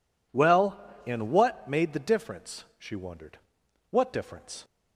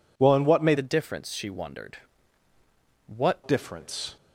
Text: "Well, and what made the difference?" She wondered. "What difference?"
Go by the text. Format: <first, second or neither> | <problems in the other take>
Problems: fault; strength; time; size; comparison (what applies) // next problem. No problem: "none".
first | changes voice from "the" to "What"; from 0.7 to 3.3 s; 2.6 s long